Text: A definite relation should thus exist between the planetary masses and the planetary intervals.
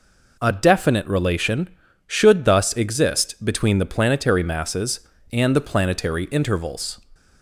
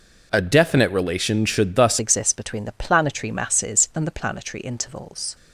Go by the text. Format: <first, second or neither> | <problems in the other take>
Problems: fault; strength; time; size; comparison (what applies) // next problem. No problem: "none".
first | changes voice at "exist"; from 1.9 s on; 3.4 s long